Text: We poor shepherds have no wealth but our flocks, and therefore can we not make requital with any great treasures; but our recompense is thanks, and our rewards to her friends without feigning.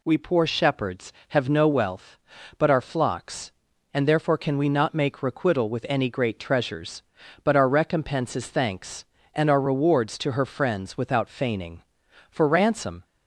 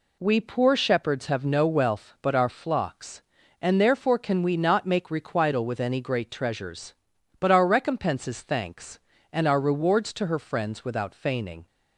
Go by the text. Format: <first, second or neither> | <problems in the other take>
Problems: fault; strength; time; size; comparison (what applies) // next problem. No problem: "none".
second | goes on to say "For ransom"; noticeable; from 12.3 s on; 0.74 s long